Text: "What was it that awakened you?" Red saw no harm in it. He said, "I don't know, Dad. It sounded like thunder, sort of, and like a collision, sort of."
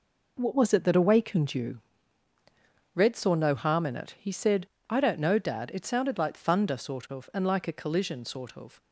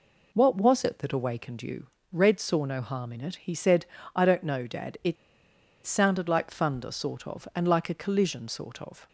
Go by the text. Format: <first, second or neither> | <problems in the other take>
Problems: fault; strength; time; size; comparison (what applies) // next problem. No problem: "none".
first | pauses between "It" and "sounded"; noticeable; at 5.1 s; 0.70 s long